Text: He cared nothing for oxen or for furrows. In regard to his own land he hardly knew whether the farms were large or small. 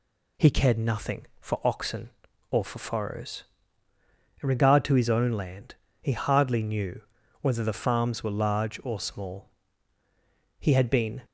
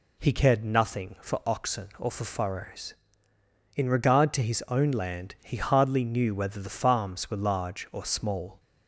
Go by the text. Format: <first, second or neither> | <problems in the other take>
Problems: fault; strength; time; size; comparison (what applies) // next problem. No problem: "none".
second | pauses between "land" and "he"; slight; at 5.7 s; 0.26 s long // pauses between "knew" and "whether"; at 7.0 s; 0.40 s long // goes on to say "He had been"; noticeable; from 10.5 s on; 0.64 s long